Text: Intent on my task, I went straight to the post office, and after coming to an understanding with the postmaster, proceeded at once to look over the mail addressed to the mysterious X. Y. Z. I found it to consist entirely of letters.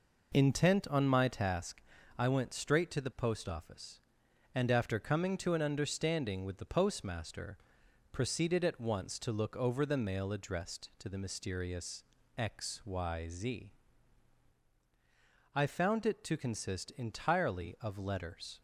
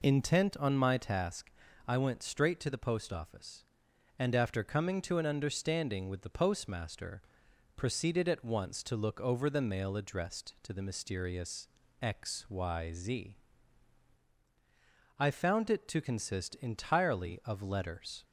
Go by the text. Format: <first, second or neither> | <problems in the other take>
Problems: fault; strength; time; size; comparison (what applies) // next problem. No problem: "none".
second | gets quieter; noticeable; throughout; 5 dB // pauses between "mysterious" and "X"; slight; at 12.0 s; 0.32 s long; slight in the second // pauses between "Z" and "I"; strong; at 13.7 s; 1.8 s long; strong in the second